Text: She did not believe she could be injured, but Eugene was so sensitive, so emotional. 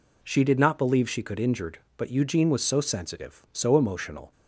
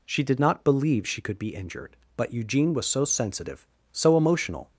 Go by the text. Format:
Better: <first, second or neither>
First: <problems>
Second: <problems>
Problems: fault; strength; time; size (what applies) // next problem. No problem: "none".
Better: second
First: skips "be"; at 1.3 s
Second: none